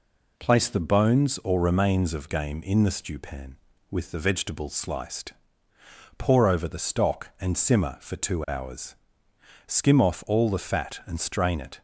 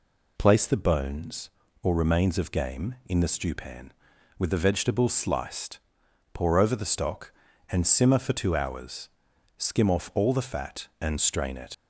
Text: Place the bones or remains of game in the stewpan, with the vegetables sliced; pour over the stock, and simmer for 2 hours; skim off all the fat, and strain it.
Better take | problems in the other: first | leaves "it" unfinished; at 11.7 s; 105 ms

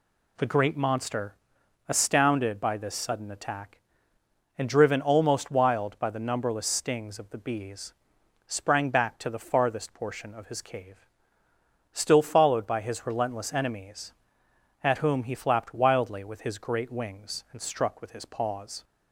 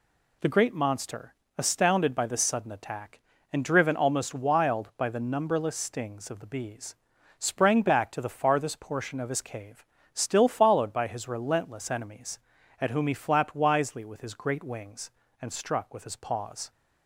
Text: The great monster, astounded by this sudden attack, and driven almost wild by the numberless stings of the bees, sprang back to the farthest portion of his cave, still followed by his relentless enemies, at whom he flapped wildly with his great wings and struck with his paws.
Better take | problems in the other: first | says "wisely" for "wildly"; at 13.5 s

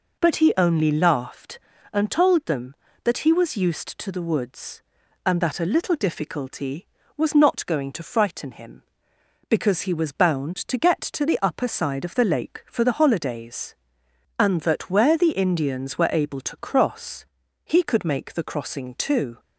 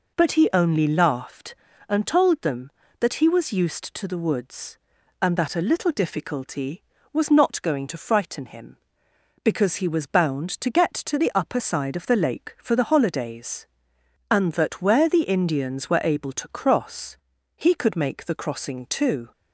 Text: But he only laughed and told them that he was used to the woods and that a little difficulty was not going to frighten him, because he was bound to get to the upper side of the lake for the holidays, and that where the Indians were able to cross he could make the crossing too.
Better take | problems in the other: neither | pauses between "cross" and "he"; the same in both

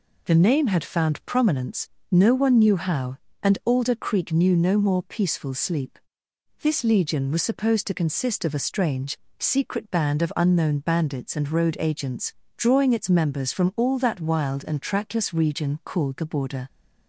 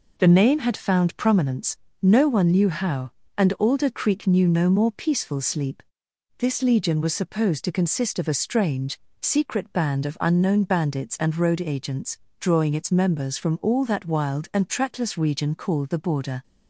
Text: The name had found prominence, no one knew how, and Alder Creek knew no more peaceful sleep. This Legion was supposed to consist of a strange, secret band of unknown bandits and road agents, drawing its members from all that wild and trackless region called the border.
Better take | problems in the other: neither | none

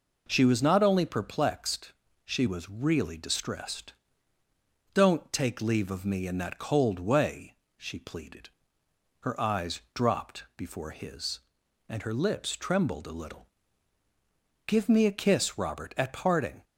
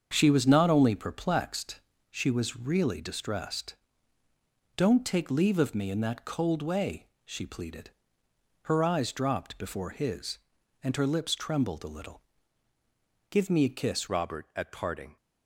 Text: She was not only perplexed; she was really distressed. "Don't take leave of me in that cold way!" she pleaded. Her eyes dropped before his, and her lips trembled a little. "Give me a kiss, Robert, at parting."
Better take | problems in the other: first | starts louder than the rest; until 1.1 s; 7 dB // changes voice at "Robert"; from 14.0 s on; 1.1 s long

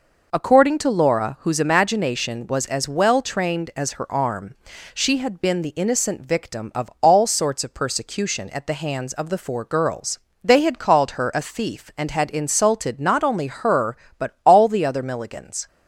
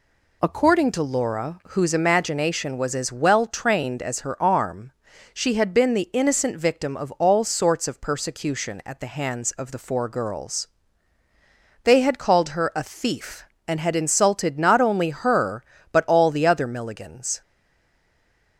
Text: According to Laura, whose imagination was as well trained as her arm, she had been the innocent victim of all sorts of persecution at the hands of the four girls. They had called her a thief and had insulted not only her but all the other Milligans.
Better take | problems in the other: first | stays silent after the last word; noticeable; from 17.4 s on; 1.1 s long

